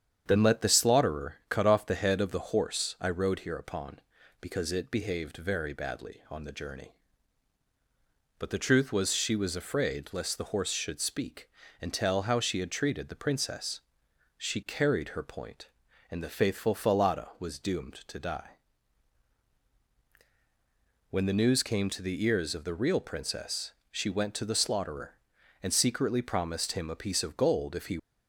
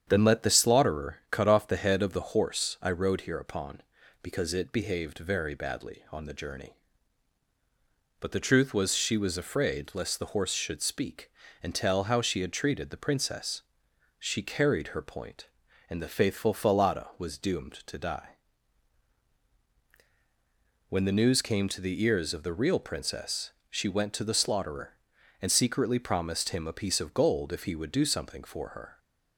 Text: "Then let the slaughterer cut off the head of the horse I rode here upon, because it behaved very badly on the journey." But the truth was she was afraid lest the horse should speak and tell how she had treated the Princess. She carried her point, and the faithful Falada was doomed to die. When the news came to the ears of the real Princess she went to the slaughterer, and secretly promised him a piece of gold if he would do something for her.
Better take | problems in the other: second | starts louder than the rest; strong; until 1.2 s; 8 dB; strong in the second // pauses between "Princess" and "she"; slight; at 23.7 s; 0.18 s long; slight in the second // stops before "would do something for her"; at 27.9 s

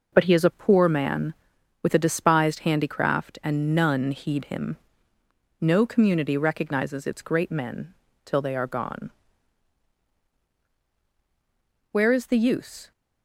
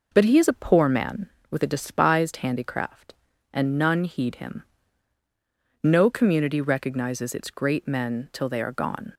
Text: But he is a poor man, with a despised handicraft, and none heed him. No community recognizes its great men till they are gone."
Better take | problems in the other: second | pauses between "men" and "till"; slight; at 7.9 s; 0.30 s long // goes on to say "Where is the use"; noticeable; from 11.9 s on; 1.0 s long

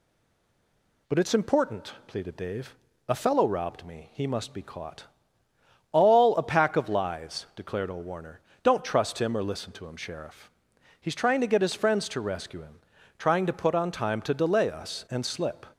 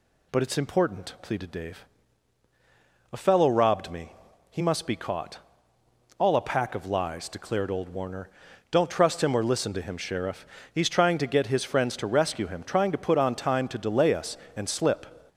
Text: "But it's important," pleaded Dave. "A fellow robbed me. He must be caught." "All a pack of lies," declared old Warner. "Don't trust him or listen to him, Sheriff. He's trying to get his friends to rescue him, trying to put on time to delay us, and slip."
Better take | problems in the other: second | stays silent before the first word; until 1.0 s; 1.0 s long

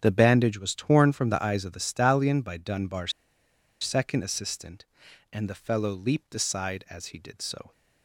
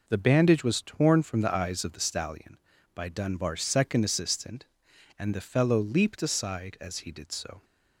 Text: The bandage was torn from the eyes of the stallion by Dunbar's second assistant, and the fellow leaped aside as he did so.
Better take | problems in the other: second | starts louder than the rest; strong; until 1.0 s; 8.5 dB // pauses between "Dunbar's" and "second"; noticeable; at 3.1 s; 0.69 s long

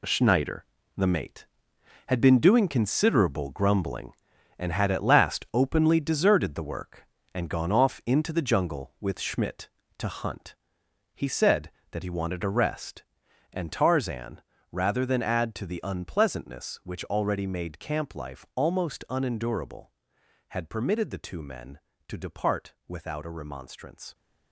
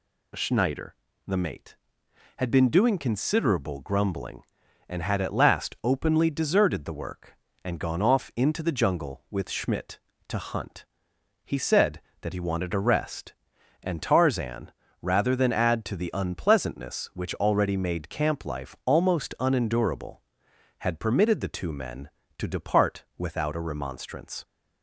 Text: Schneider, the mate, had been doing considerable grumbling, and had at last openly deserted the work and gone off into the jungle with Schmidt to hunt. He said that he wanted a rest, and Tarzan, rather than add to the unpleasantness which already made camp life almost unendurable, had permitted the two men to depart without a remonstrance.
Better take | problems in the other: second | gets quieter; strong; throughout; 10.5 dB

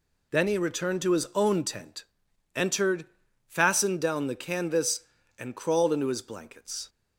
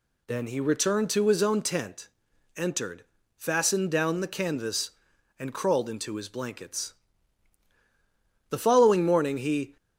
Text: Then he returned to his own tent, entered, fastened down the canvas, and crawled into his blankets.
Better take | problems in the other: first | goes on to say "The following morning he"; noticeable; from 8.5 s on; 1.2 s long

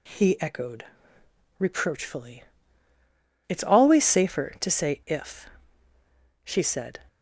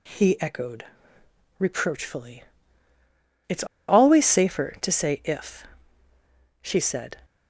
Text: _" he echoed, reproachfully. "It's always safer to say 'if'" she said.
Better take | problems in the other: first | pauses between "It's" and "always"; slight; at 3.6 s; 0.23 s long // pauses between "if" and "she"; noticeable; at 5.6 s; 0.98 s long; noticeable in the first

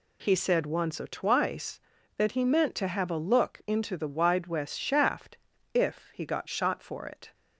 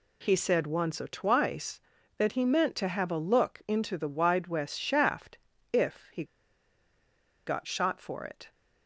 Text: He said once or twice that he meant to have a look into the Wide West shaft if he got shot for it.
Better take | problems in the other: first | pauses between "shaft" and "if"; slight; at 5.3 s; 0.34 s long; slight in the first // pauses between "he" and "got"; at 6.2 s; 1.2 s long

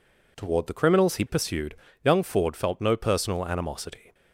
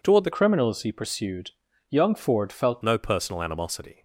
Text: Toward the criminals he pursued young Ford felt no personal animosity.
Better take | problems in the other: first | changes voice from "criminals" to "felt"; from 0.3 to 2.8 s; 2.5 s long // pauses between "pursued" and "young"; at 1.5 s; 0.40 s long; slight in the first

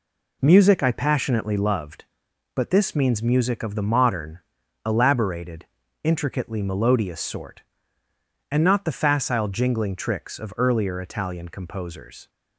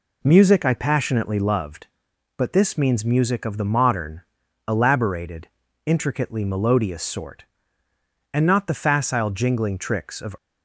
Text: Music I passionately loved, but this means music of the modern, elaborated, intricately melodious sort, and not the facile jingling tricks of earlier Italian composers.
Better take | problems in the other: first | stops before "earlier Italian composers"; at 10.3 s

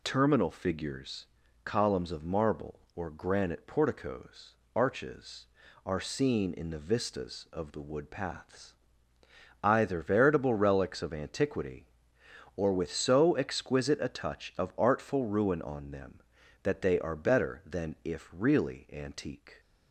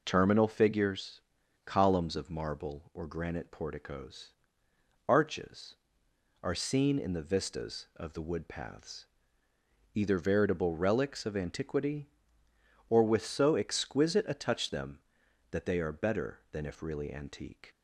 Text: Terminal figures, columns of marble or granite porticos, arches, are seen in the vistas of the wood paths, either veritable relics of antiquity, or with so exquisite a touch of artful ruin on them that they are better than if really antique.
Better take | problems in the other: first | skips "of artful ruin on"; at 14.7 s

